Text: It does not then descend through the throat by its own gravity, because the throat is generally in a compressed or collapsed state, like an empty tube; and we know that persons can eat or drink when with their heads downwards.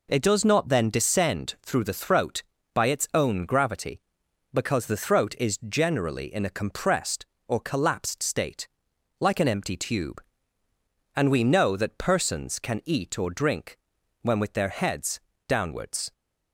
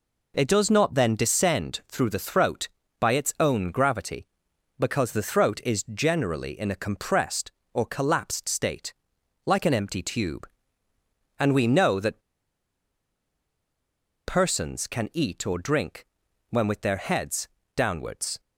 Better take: first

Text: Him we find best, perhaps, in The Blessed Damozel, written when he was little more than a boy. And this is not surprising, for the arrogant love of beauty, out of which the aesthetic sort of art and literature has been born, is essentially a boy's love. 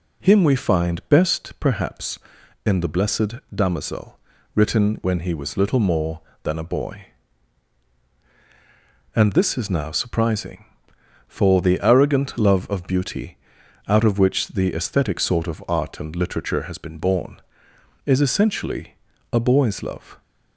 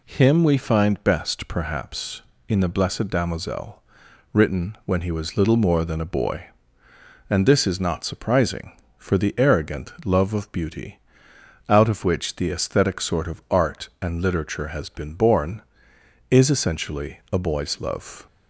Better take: second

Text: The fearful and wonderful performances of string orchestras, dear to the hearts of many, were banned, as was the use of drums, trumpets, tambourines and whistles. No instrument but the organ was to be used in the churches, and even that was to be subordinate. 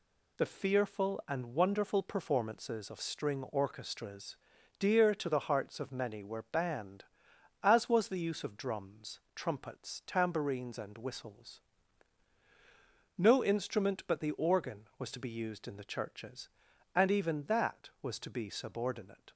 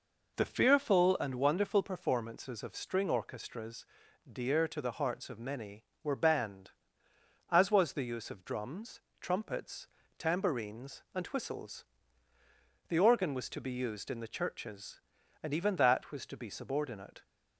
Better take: first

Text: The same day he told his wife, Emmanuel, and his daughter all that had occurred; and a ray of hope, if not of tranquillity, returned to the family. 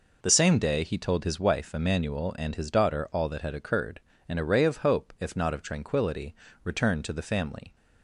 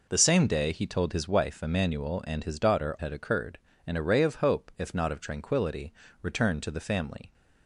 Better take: first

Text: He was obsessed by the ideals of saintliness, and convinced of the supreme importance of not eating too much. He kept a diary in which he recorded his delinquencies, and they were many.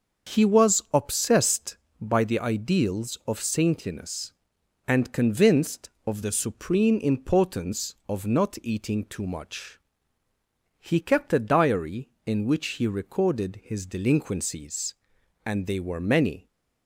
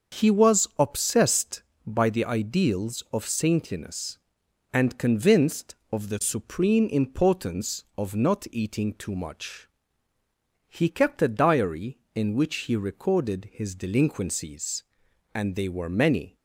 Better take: neither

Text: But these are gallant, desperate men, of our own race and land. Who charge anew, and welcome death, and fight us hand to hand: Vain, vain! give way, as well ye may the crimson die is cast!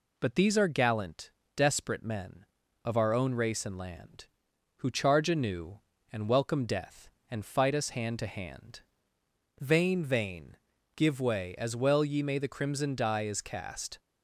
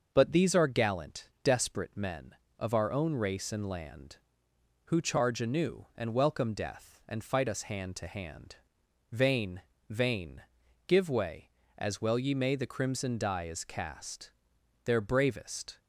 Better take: first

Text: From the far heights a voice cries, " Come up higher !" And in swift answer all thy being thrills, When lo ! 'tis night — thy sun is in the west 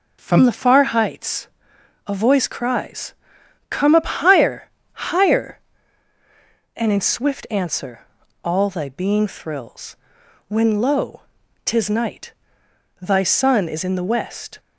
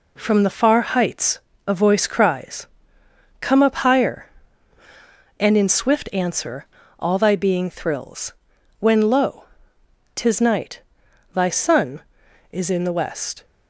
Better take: second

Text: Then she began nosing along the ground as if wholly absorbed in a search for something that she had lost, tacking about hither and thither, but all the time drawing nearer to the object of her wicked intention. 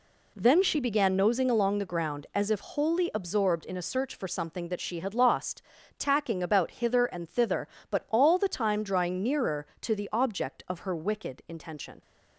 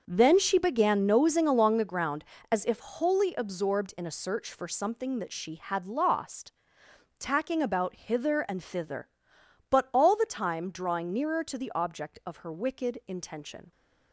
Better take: first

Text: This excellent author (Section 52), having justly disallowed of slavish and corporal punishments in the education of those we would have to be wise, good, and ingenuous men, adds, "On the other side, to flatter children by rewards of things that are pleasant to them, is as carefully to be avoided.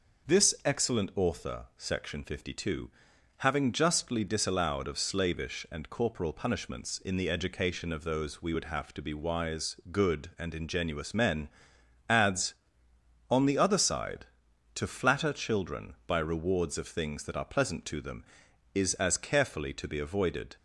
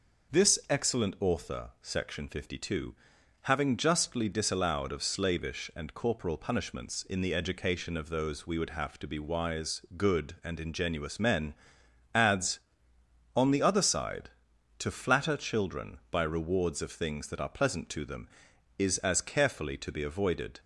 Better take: neither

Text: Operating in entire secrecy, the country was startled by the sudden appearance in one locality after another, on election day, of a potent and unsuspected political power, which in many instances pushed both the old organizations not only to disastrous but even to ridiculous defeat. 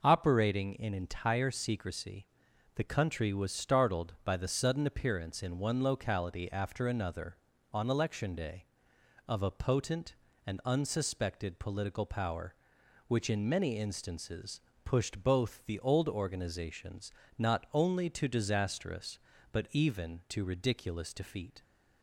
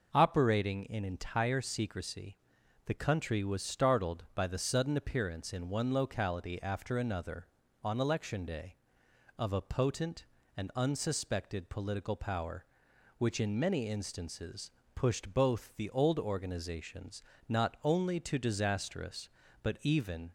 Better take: first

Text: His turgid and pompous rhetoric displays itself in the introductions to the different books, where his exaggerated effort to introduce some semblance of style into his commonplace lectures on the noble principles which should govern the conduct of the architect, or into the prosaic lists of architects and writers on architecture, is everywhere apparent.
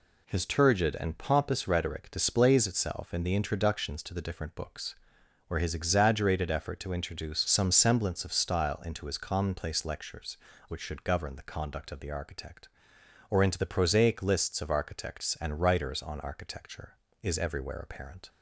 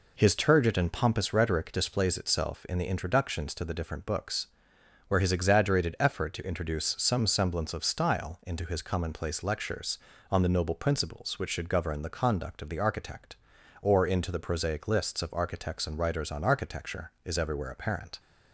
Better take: second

